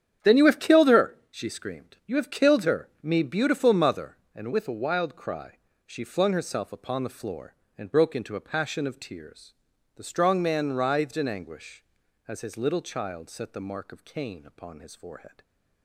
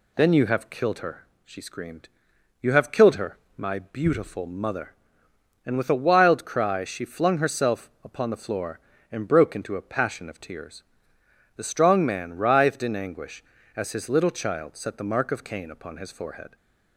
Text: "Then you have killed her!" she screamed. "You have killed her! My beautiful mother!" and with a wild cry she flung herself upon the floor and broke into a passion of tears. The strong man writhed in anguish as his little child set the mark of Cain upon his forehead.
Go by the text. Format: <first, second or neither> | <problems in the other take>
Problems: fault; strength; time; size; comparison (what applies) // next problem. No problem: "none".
second | starts louder than the rest; strong; until 1.3 s; 9 dB // says "Me" for "My"; at 3.0 s // pauses between "cry" and "she"; slight; at 5.5 s; 0.28 s long